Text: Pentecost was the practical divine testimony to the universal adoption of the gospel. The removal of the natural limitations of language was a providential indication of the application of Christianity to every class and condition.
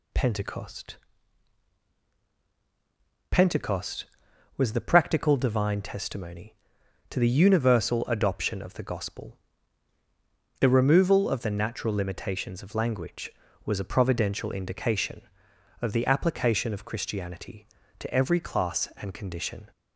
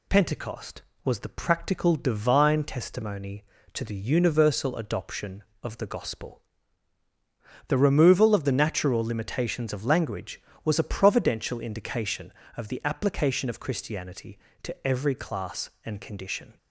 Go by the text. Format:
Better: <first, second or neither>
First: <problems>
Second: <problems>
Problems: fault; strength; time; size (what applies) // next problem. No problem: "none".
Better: second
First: says "Pentecost" twice; at 3.3 s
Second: none